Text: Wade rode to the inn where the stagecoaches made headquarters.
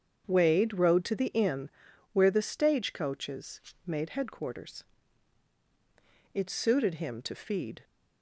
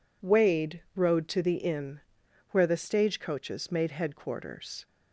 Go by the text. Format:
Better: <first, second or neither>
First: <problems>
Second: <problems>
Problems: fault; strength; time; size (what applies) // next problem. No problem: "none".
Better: second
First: starts louder than the rest; strong; until 1.2 s; 7.5 dB // pauses between "inn" and "where"; noticeable; at 1.6 s; 0.46 s long // pauses between "stagecoaches" and "made"; slight; at 3.6 s; 0.24 s long // goes on to say "It suited him to feed"; from 6.3 s on; 1.5 s long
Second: pauses between "inn" and "where"; noticeable; at 2.0 s; 0.52 s long